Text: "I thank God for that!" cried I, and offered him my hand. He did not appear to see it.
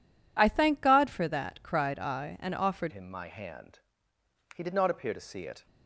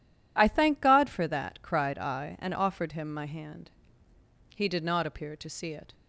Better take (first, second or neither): second